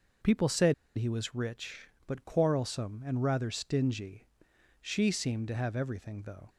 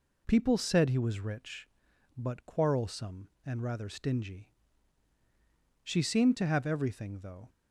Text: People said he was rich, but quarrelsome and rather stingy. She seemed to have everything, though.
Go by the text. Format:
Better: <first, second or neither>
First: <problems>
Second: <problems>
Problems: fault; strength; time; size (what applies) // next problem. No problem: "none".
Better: second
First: pauses between "said" and "he"; slight; at 0.7 s; 0.22 s long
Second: none